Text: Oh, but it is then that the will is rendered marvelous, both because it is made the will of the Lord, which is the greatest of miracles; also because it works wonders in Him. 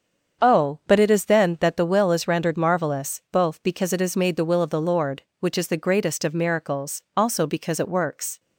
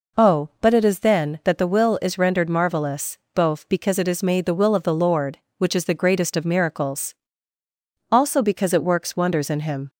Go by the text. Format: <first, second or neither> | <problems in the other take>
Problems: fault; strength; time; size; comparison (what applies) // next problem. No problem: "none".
second | starts louder than the rest; strong; until 1.5 s; 7 dB // stops before "wonders in Him"; at 8.3 s